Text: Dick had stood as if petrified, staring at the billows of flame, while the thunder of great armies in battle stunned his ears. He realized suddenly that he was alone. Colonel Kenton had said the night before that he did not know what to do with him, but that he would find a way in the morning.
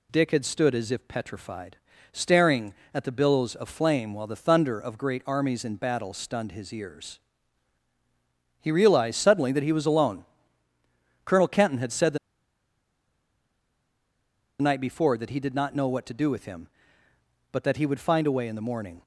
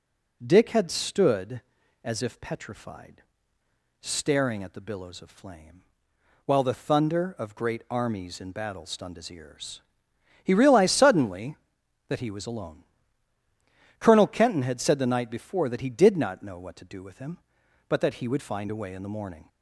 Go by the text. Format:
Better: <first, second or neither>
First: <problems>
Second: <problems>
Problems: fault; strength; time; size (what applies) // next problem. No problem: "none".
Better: second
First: pauses between "the" and "night"; strong; at 12.1 s; 2.4 s long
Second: none